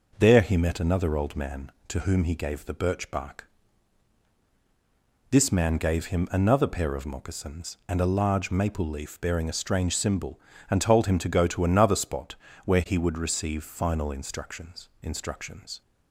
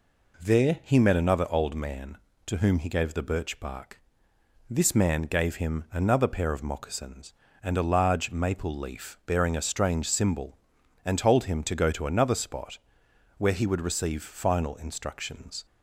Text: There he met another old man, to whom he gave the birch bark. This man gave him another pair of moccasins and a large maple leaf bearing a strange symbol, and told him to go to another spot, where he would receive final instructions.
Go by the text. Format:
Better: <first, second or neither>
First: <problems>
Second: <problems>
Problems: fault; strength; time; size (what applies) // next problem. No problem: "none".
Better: second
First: says "instructions" twice; at 15.0 s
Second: none